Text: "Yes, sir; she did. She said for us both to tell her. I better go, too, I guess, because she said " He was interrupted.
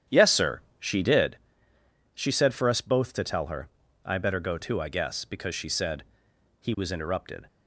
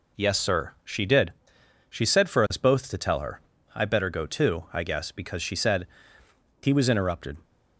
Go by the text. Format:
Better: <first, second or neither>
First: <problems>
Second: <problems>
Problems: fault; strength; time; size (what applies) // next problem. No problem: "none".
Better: second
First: starts louder than the rest; strong; until 1.3 s; 10 dB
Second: none